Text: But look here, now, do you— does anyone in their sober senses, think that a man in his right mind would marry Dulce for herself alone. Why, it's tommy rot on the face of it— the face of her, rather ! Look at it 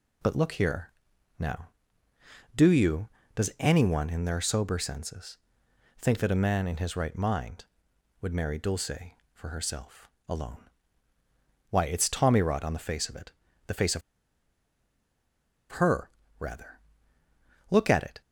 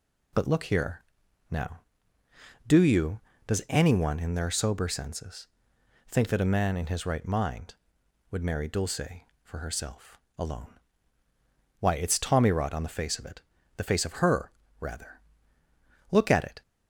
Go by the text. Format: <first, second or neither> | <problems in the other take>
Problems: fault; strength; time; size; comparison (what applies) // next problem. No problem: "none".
second | pauses between "herself" and "alone"; slight; at 10.0 s; 0.20 s long; slight in the second // pauses between "of" and "her"; strong; at 14.0 s; 1.7 s long